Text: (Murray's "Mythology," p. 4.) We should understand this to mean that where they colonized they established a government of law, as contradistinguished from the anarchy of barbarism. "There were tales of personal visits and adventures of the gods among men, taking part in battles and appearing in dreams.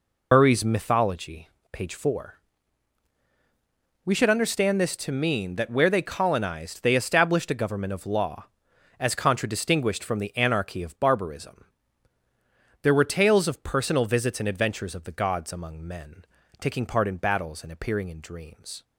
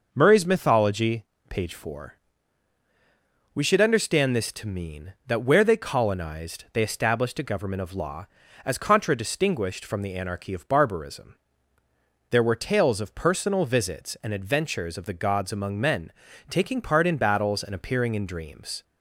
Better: second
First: loses the start of "Murray's"; at 0.3 s; 80 ms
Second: none

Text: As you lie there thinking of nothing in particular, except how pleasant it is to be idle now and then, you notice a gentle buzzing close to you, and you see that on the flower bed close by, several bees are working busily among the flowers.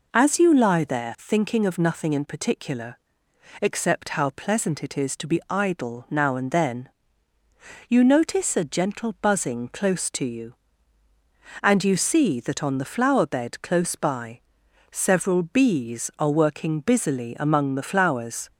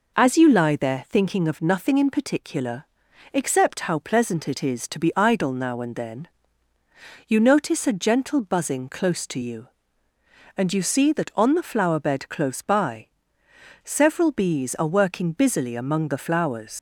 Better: first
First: none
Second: leaves "flowers" unfinished; at 16.7 s; 115 ms

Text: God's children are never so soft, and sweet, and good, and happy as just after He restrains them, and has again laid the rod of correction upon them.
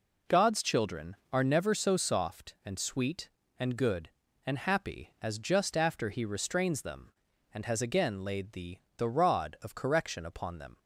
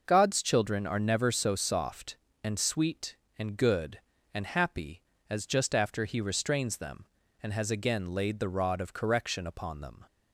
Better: second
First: says "the" twice; at 8.9 s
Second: none

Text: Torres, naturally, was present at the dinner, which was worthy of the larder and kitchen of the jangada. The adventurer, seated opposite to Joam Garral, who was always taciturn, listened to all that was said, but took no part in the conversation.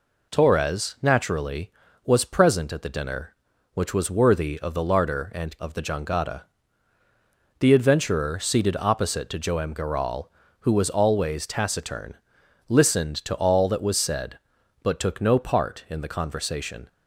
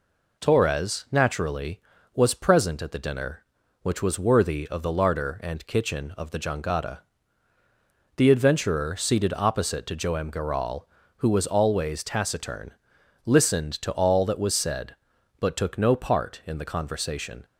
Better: second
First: skips "kitchen"; at 5.5 s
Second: none

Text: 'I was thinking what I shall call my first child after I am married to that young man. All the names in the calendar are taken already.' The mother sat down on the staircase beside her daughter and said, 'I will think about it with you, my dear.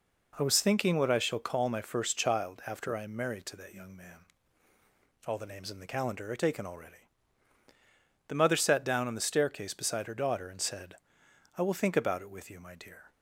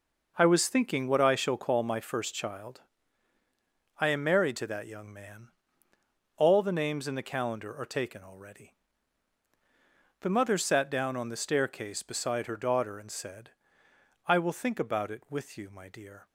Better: first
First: none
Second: skips "after"; at 3.4 s

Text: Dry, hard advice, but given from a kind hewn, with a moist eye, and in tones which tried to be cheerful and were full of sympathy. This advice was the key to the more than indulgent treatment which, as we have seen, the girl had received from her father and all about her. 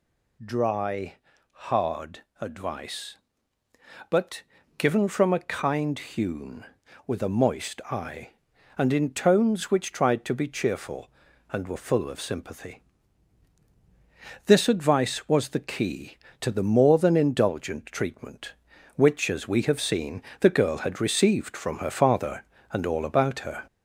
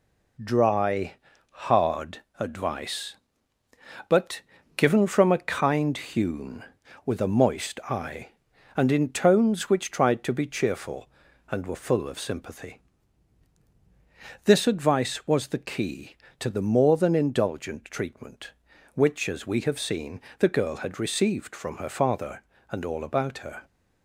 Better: second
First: gets louder; slight; throughout; 3 dB // pauses between "hard" and "advice"; slight; at 2.2 s; 0.18 s long // pauses between "but" and "given"; slight; at 4.4 s; 0.36 s long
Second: pauses between "hard" and "advice"; slight; at 2.2 s; 0.18 s long // pauses between "but" and "given"; slight; at 4.4 s; 0.36 s long

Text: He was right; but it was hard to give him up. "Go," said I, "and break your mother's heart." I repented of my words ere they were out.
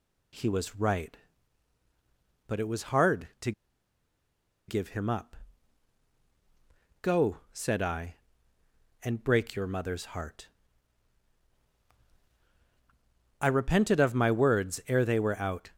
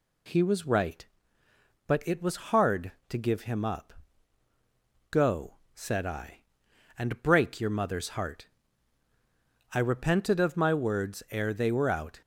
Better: second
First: pauses between "to" and "give"; at 3.5 s; 1.1 s long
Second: none

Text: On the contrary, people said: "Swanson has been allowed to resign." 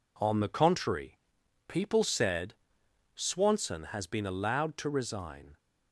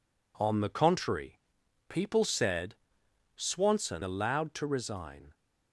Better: first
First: none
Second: skips "has been"; at 4.0 s

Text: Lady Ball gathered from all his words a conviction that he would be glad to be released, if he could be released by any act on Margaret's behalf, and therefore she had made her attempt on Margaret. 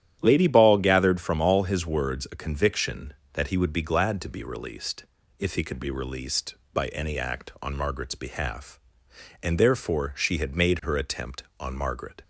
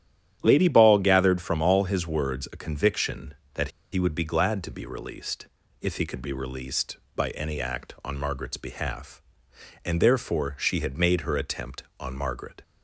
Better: first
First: starts louder than the rest; strong; until 1.2 s; 11 dB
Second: starts louder than the rest; strong; until 1.4 s; 10.5 dB // pauses between "that" and "he"; slight; at 3.6 s; 0.24 s long

